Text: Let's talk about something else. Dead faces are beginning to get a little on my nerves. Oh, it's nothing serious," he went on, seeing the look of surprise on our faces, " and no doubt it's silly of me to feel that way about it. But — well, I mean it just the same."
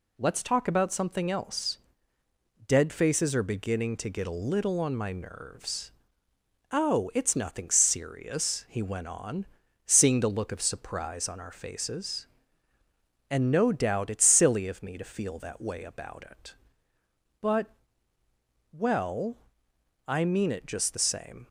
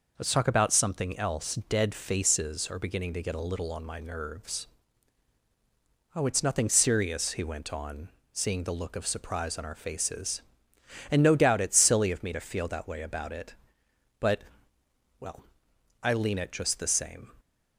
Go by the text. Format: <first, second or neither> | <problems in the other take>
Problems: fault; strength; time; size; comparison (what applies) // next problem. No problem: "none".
first | says "lean" for "mean"; at 16.1 s